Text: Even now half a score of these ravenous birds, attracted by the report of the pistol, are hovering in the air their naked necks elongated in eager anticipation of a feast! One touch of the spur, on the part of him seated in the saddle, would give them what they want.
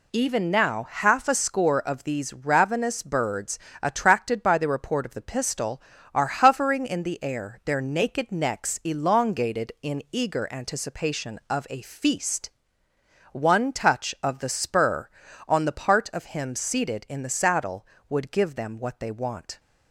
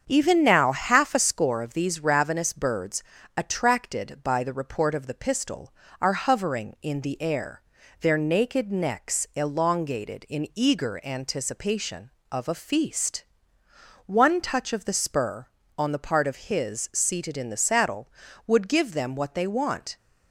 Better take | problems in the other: first | starts louder than the rest; strong; until 1.0 s; 7.5 dB // pauses between "air" and "their"; at 7.6 s; 0.38 s long // says "his" for "him"; at 16.4 s

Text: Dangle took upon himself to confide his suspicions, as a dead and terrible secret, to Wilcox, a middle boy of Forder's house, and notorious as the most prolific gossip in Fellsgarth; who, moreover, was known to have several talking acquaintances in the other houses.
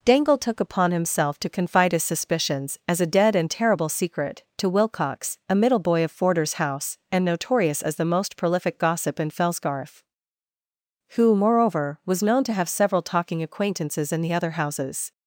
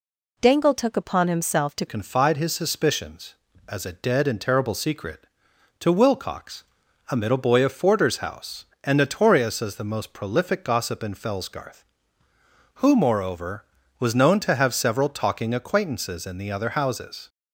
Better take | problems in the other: first | changes voice at "confide"; from 1.8 s on; 15.4 s long

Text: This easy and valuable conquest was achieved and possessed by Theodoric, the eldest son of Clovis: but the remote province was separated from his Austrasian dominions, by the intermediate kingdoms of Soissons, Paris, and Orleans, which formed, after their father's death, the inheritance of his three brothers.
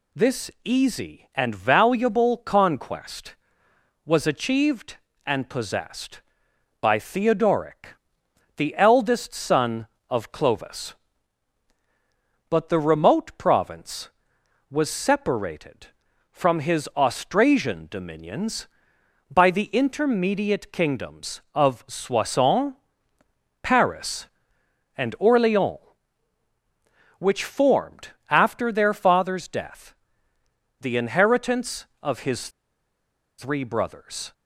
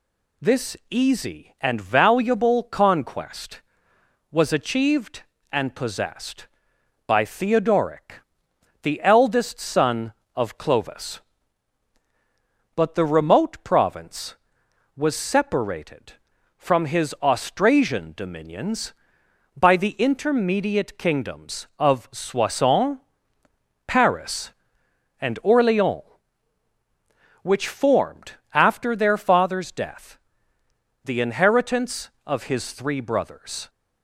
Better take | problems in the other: second | pauses between "his" and "three"; noticeable; at 32.4 s; 0.88 s long

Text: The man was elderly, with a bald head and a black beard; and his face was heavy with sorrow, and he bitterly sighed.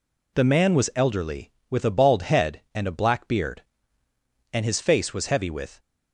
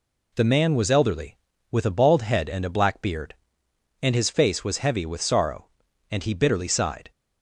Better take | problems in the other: second | stops before "sorrow and he bitterly sighed"; at 5.7 s

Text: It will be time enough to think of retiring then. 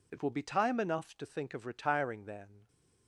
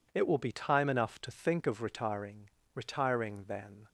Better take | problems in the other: first | says "retiring" twice; at 2.7 s

